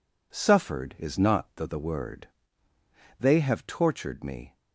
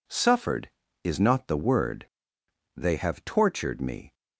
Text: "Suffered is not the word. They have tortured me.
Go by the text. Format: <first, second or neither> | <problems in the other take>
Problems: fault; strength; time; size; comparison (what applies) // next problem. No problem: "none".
second | says "the" twice; at 1.6 s